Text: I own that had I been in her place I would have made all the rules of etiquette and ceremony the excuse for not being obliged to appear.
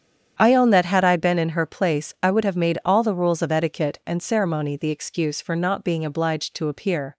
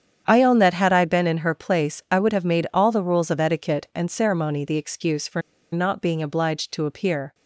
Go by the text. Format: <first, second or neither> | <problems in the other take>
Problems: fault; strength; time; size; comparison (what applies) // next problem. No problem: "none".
first | starts louder than the rest; strong; until 1.2 s; 8.5 dB; strong in the first // pauses between "for" and "not"; slight; at 5.4 s; 0.33 s long